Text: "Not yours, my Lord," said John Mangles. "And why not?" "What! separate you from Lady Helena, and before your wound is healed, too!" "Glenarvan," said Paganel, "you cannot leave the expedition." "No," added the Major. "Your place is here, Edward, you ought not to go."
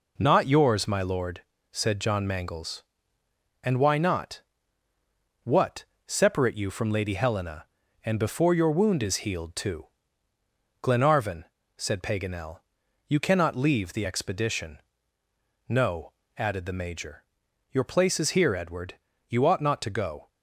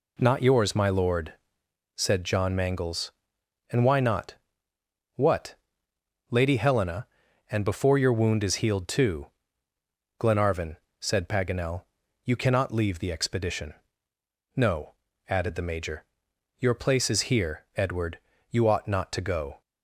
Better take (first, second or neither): first